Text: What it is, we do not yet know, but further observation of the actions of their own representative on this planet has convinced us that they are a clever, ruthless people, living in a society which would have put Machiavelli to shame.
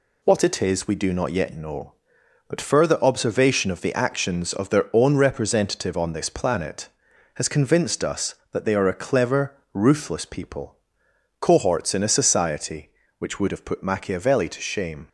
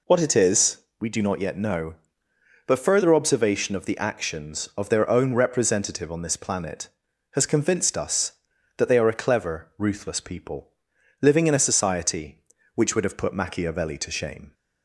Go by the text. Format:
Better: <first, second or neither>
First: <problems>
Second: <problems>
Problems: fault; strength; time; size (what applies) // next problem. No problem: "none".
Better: second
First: says "cohorts" for "living"; at 11.3 s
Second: none